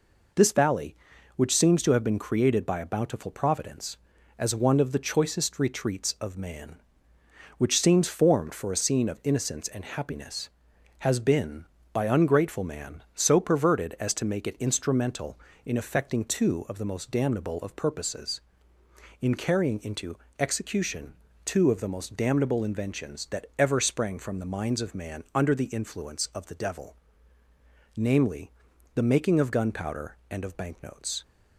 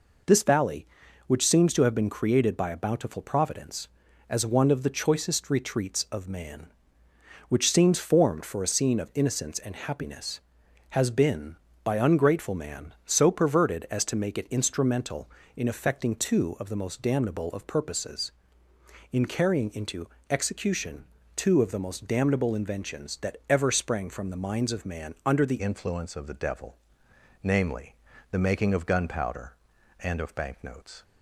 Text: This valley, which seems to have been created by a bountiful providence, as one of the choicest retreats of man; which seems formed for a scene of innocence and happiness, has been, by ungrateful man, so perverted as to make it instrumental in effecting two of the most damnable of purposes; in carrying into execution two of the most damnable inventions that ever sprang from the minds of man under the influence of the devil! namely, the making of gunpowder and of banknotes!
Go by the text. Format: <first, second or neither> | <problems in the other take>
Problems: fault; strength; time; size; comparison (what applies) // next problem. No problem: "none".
first | pauses between "into" and "execution"; slight; at 20.0 s; 0.22 s long; slight in the first // pauses between "execution" and "two"; slight; at 21.0 s; 0.32 s long; slight in the first // changes voice at "influence"; from 25.6 s on; 5.4 s long